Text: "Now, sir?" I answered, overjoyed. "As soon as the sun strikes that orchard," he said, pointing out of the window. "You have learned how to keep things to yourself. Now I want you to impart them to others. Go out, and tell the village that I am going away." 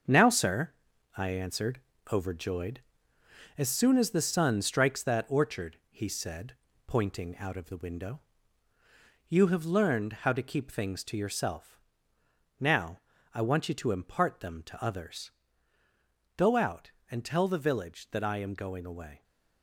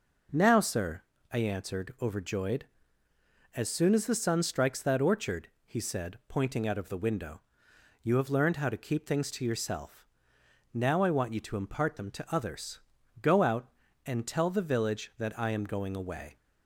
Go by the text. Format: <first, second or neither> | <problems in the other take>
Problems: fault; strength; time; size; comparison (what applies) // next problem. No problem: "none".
second | gets quieter; strong; throughout; 7.5 dB // pauses between "Now" and "I"; slight; at 12.9 s; 0.34 s long